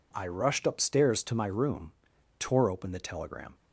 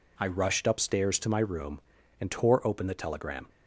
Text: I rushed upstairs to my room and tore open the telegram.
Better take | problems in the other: second | skips "and"; at 2.1 s

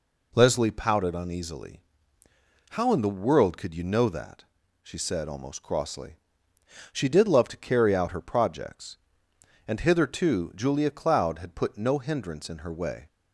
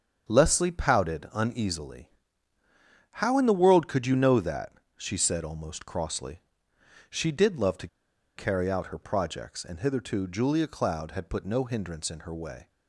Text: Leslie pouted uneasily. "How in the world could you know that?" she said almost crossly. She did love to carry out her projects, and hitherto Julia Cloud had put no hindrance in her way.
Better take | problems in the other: first | starts louder than the rest; strong; until 1.3 s; 7.5 dB // pauses between "to" and "carry"; noticeable; at 7.8 s; 0.49 s long

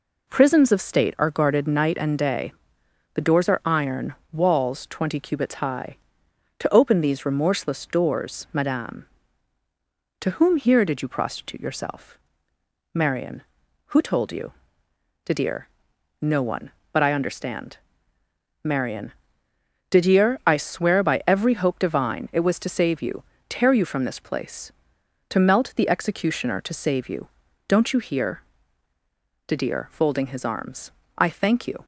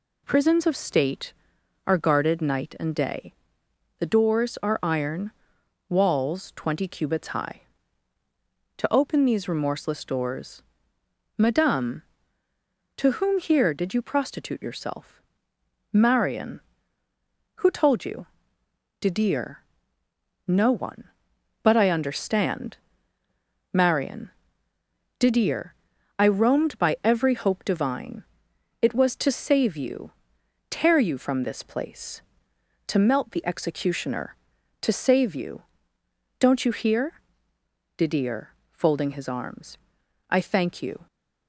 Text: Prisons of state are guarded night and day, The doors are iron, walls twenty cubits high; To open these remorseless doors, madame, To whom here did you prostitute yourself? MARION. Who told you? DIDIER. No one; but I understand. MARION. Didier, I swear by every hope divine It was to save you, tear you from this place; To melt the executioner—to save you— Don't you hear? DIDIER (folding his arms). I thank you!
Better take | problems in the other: first | says "roamed" for "swear"; at 26.2 s // pauses between "divine" and "It"; noticeable; at 28.2 s; 0.56 s long

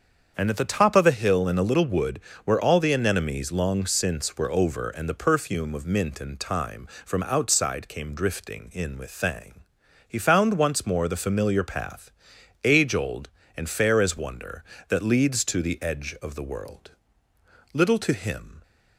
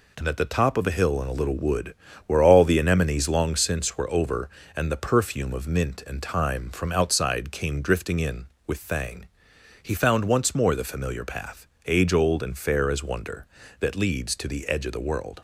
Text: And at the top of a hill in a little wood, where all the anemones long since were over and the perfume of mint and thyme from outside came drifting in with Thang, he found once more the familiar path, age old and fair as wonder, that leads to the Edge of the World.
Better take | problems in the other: second | starts louder than the rest; strong; until 1.3 s; 7 dB // goes on to say "Little to him"; noticeable; from 17.7 s on; 0.88 s long

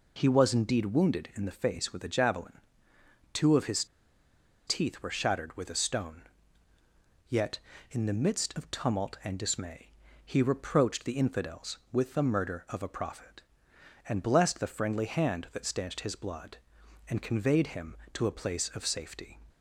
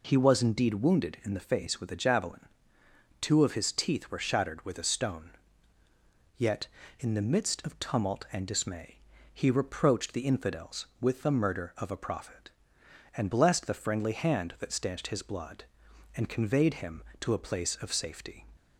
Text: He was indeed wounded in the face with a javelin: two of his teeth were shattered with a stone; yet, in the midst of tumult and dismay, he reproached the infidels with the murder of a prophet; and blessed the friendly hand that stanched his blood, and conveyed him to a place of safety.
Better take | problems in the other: second | pauses between "his" and "teeth"; noticeable; at 3.8 s; 0.82 s long

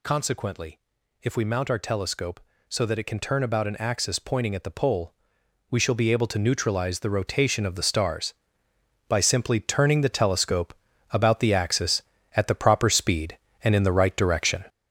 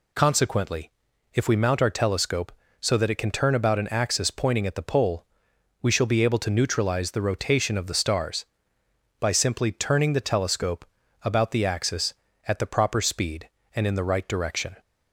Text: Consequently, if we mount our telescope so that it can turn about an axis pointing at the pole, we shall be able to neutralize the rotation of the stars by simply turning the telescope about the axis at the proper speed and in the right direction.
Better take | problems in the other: second | gets louder; noticeable; throughout; 6 dB // pauses between "telescope" and "about"; at 10.7 s; 0.38 s long; also in the second

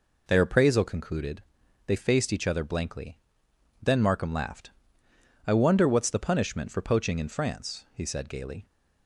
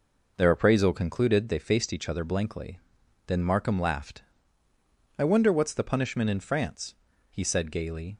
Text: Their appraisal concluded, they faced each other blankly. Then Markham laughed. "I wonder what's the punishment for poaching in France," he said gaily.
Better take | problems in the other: first | skips "for poaching"; at 6.3 s

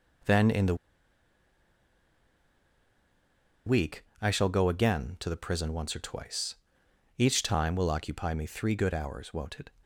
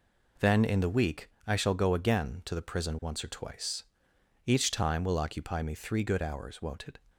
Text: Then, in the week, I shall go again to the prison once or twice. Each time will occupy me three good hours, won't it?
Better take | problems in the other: second | pauses between "the" and "week"; strong; at 0.7 s; 2.9 s long

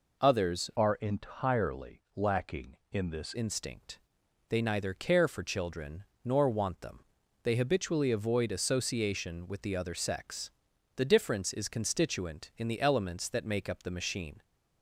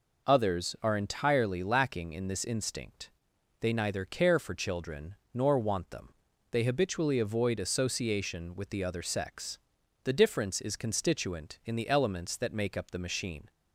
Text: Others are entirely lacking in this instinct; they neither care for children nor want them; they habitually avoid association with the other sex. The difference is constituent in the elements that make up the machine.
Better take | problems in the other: second | changes voice from "are" to "this"; from 0.7 to 3.3 s; 2.6 s long // pauses between "children" and "nor"; slight; at 6.0 s; 0.18 s long; slight in the second

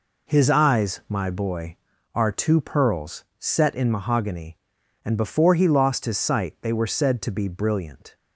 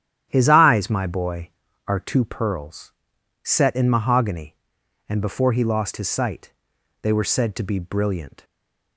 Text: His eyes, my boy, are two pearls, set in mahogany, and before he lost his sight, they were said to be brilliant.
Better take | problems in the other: first | starts louder than the rest; strong; until 1.3 s; 10.5 dB // stays silent after the last word; slight; from 8.4 s on; 0.5 s long

